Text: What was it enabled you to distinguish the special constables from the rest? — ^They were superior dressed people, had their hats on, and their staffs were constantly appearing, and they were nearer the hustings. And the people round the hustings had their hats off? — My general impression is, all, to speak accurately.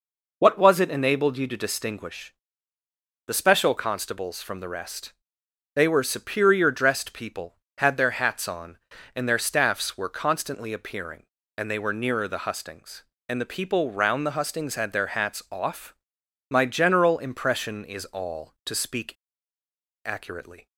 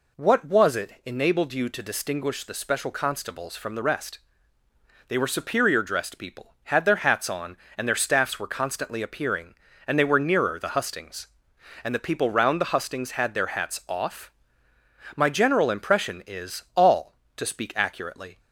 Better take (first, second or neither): second